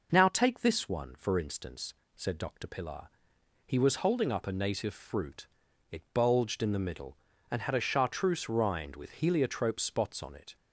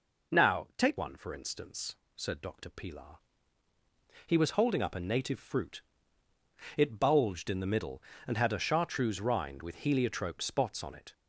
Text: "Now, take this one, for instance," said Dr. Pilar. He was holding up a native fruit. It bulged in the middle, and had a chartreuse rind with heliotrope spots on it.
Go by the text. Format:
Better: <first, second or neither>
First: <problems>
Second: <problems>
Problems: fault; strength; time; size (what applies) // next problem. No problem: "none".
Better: first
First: none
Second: skips "this"; at 0.9 s